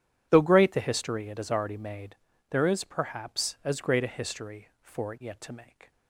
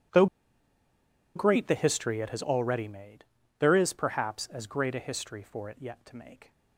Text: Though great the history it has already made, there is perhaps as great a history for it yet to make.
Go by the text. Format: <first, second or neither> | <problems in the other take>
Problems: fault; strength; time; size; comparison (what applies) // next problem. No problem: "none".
first | pauses between "Though" and "great"; at 0.2 s; 1.1 s long